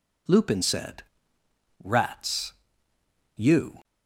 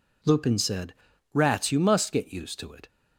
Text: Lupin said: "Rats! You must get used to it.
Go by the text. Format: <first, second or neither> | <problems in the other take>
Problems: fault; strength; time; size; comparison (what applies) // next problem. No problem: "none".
second | stops before "must get used to it"; at 3.8 s